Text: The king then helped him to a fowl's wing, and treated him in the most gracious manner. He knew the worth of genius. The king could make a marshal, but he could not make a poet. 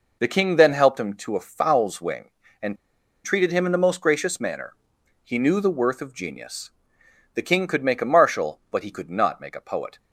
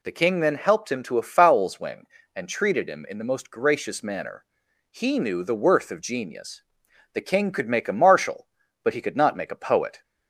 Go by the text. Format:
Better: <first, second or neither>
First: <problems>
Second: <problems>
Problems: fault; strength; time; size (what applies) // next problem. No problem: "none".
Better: second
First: pauses between "and" and "treated"; noticeable; at 2.7 s; 0.48 s long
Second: none